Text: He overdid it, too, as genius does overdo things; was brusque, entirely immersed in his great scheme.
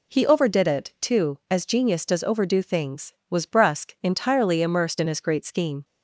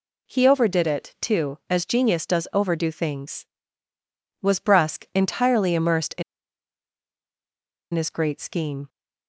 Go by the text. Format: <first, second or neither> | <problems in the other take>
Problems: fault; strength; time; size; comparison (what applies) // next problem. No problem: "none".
first | pauses between "in" and "his"; strong; at 6.2 s; 1.7 s long